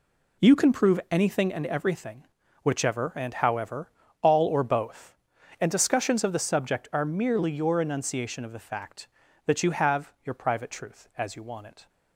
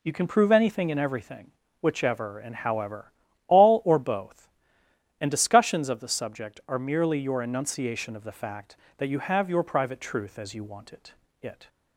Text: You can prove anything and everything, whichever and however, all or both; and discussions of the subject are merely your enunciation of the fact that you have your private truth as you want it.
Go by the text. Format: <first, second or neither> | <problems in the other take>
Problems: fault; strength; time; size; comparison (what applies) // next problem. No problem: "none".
first | says "it" twice; at 11.4 s